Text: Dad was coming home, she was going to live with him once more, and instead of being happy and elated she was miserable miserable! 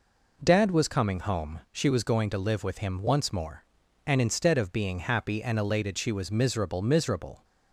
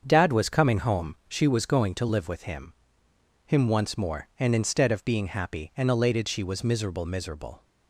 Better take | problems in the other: first | starts louder than the rest; until 1.0 s; 7 dB // says "him" twice; at 3.4 s

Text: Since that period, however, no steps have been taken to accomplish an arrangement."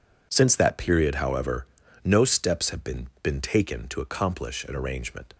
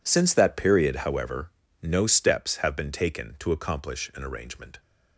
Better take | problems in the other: second | says "been" twice; at 3.2 s

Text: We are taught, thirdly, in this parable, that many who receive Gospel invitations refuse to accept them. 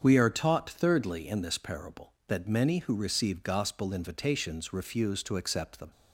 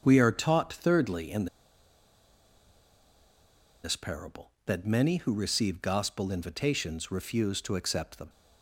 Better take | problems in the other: first | starts louder than the rest; strong; until 1.0 s; 7 dB; strong in the first // pauses between "in" and "this"; strong; at 1.4 s; 2.3 s long

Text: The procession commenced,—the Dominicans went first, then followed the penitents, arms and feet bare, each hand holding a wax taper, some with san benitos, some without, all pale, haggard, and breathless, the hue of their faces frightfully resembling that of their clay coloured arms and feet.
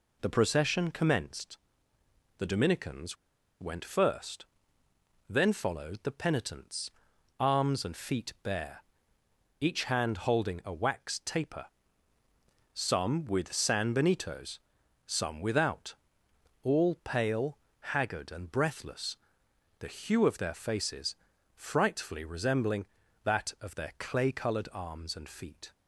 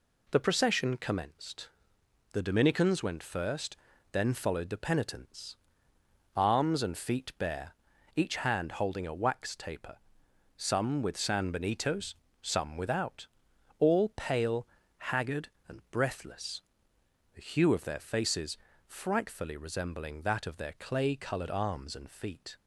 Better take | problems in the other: second | pauses between "Dominicans" and "went"; at 3.1 s; 0.45 s long // pauses between "faces" and "frightfully"; at 21.1 s; 0.40 s long; slight in the second

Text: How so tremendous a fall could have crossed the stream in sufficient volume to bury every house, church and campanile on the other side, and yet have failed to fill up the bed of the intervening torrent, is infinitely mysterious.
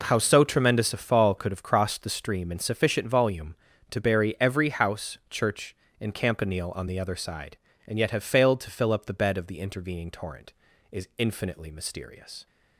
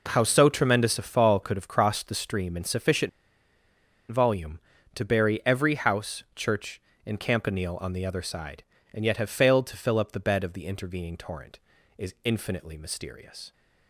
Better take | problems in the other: first | pauses between "sufficient" and "volume"; at 3.0 s; 1.0 s long

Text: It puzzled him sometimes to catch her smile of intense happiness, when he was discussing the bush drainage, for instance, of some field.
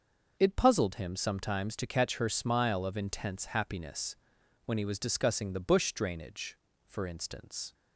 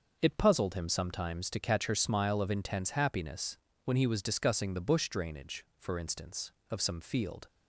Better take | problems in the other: second | starts louder than the rest; noticeable; until 1.4 s; 6 dB; noticeable in the second // stops before "of some field"; at 7.7 s

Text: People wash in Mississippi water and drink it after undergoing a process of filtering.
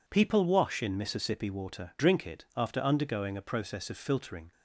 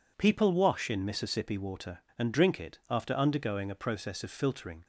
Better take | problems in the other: second | skips "and"; at 1.9 s

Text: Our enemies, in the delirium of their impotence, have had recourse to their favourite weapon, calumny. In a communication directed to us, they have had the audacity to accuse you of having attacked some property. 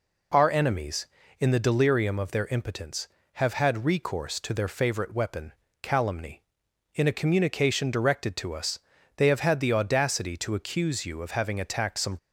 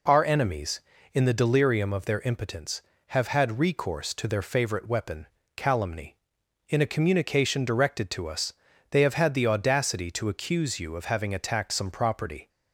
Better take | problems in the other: second | stops before "property"; at 12.1 s

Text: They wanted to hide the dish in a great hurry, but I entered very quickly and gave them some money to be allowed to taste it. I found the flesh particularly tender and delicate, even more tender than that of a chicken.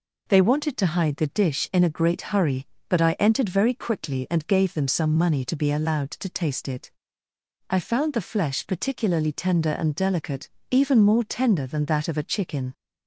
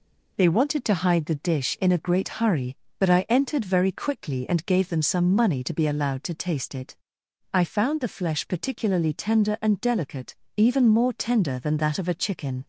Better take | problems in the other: neither | none

